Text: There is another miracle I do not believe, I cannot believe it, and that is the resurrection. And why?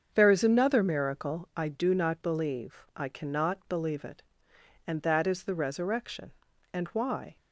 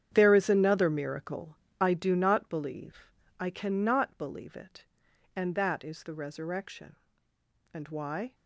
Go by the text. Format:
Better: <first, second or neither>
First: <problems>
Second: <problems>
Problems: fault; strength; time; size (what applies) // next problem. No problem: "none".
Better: first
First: starts louder than the rest; until 1.1 s; 7 dB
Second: gets quieter; strong; throughout; 12.5 dB // starts louder than the rest; strong; until 1.1 s; 9 dB // pauses between "miracle" and "I"; slight; at 1.5 s; 0.24 s long